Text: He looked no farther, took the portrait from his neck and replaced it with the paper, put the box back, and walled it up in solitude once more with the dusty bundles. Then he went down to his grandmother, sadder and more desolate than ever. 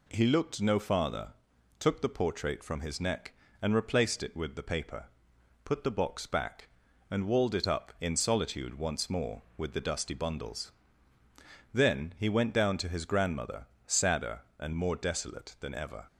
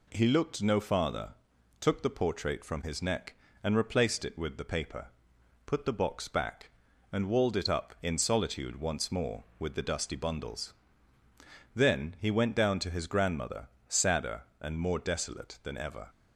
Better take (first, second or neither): neither